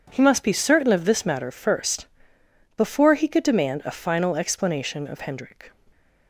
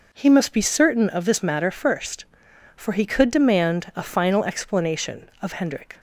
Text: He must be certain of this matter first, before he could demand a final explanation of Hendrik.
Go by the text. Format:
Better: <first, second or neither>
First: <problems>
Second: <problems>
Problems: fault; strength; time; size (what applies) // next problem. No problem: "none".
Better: first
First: none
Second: says "for" for "before"; at 2.7 s